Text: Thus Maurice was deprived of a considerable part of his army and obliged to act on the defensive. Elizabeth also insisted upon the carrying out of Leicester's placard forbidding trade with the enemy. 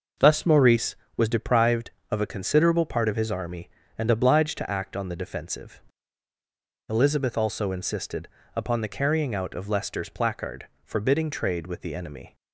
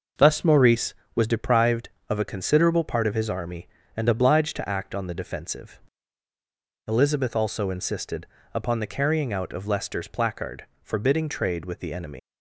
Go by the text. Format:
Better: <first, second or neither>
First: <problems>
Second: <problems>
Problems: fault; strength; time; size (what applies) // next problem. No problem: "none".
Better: first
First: pauses between "insisted" and "upon"; slight; at 8.2 s; 0.28 s long // pauses between "placard" and "forbidding"; slight; at 10.6 s; 0.18 s long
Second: pauses between "insisted" and "upon"; slight; at 8.2 s; 0.28 s long // pauses between "placard" and "forbidding"; slight; at 10.6 s; 0.18 s long // leaves "enemy" unfinished; at 12.1 s; 135 ms